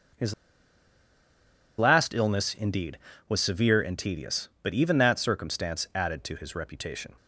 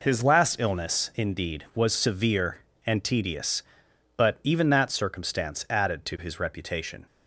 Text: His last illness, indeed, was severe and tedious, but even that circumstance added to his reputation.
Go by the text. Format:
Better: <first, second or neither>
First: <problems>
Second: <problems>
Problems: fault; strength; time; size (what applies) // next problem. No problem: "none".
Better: second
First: starts louder than the rest; until 2.6 s; 6.5 dB // pauses between "His" and "last"; strong; at 0.3 s; 1.4 s long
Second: none